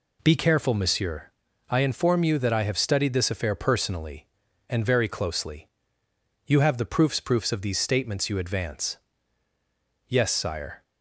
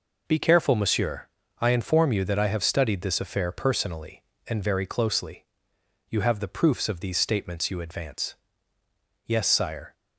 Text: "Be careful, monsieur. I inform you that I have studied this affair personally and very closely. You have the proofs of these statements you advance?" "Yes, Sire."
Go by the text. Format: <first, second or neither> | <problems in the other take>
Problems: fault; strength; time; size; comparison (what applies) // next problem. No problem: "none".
second | says "proofs" twice; at 7.2 s